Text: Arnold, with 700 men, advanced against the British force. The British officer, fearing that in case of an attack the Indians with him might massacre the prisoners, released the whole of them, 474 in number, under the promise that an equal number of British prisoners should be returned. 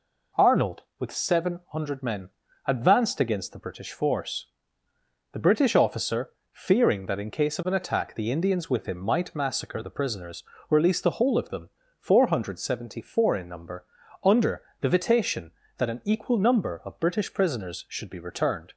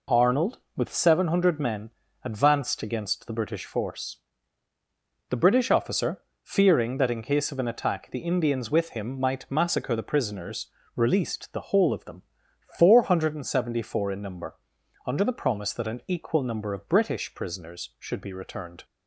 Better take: second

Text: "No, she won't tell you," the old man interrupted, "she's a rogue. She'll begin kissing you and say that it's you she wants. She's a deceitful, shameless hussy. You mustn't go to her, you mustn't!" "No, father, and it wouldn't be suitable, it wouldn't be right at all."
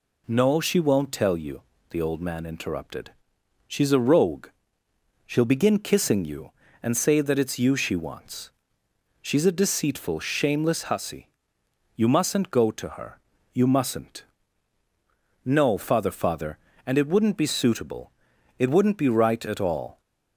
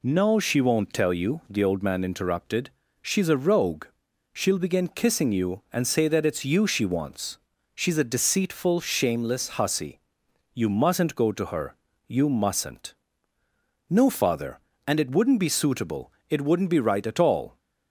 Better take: second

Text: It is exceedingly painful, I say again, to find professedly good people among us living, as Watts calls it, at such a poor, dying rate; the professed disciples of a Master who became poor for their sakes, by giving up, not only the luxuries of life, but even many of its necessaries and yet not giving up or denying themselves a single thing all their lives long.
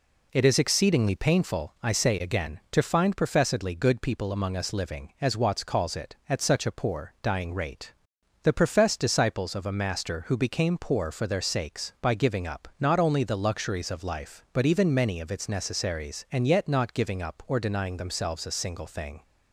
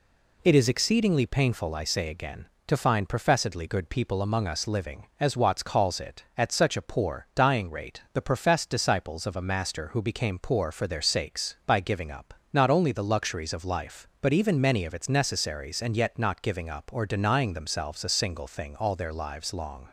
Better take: second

